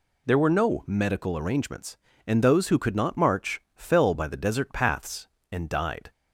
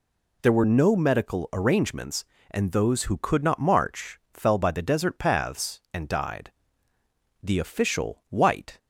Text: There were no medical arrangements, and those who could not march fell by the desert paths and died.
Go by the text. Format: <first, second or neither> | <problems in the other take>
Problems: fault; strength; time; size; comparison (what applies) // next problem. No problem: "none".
first | goes on to say "The official White"; from 7.4 s on; 1.3 s long